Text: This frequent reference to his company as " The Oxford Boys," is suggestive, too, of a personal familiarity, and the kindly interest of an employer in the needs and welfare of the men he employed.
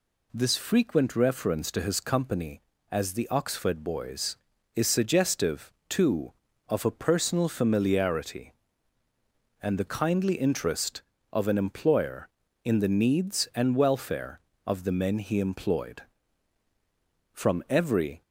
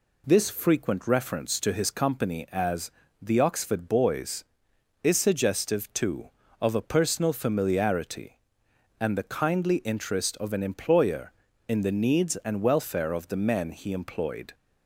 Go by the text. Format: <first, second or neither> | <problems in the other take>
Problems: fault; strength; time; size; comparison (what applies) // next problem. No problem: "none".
second | goes on to say "From every"; noticeable; from 17.3 s on; 0.90 s long